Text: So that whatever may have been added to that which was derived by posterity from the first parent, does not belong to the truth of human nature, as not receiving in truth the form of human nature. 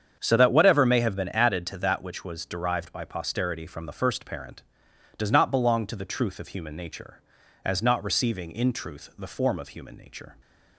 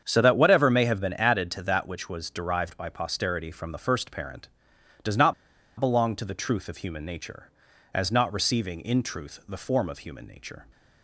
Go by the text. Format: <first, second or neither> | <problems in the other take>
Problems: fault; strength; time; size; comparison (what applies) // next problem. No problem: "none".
first | starts louder than the rest; strong; until 1.0 s; 7.5 dB; strong in the first // pauses between "not" and "belong"; noticeable; at 5.3 s; 0.46 s long